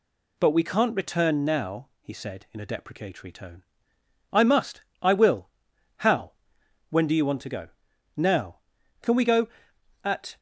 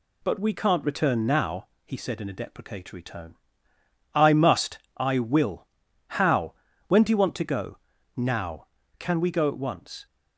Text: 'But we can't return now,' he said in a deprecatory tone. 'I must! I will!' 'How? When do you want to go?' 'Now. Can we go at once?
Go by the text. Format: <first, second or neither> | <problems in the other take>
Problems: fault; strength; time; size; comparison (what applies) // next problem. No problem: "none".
second | stops before "once"; at 10.3 s